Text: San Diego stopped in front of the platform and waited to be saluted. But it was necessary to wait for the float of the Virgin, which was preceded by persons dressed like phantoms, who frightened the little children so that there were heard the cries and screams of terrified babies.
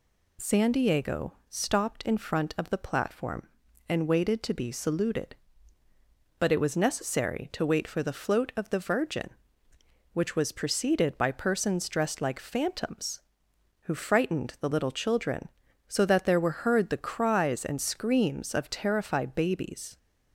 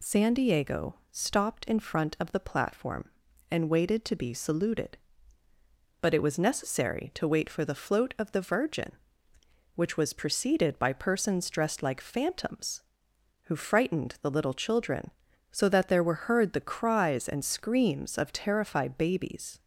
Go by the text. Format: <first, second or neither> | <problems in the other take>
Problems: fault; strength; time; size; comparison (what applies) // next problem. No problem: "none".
neither | pauses between "Diego" and "stopped"; slight; the same in both